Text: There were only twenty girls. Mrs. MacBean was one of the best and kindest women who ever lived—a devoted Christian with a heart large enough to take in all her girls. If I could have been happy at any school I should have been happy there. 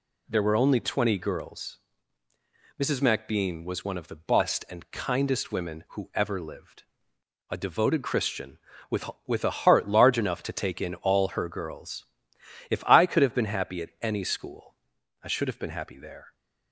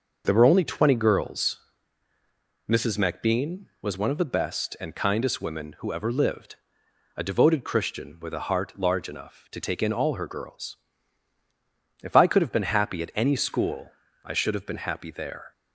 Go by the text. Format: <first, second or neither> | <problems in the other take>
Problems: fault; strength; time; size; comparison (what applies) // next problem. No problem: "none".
second | says "with" twice; at 9.2 s // pauses between "school" and "I"; noticeable; at 14.7 s; 0.50 s long; slight in the second